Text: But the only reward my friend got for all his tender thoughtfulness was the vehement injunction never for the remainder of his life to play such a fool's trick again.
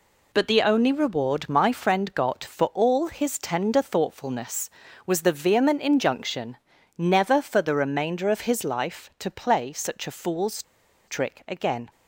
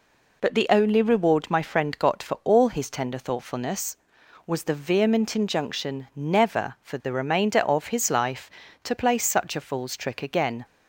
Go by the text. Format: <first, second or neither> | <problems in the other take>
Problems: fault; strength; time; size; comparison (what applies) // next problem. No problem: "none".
second | pauses between "injunction" and "never"; at 6.5 s; 0.40 s long // pauses between "fool's" and "trick"; at 10.6 s; 0.44 s long